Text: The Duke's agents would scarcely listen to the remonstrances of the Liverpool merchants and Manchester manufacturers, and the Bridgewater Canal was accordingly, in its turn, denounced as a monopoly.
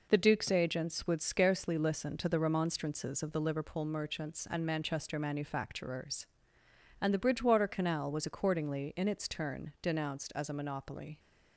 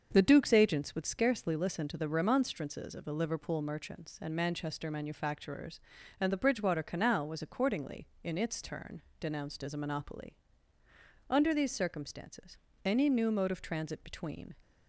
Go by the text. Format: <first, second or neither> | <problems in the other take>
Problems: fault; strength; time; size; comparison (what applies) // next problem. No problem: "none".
first | starts louder than the rest; until 1.1 s; 6.5 dB // goes on to say "Under these circumstances any new mode of transit between"; strong; from 11.2 s on; 3.2 s long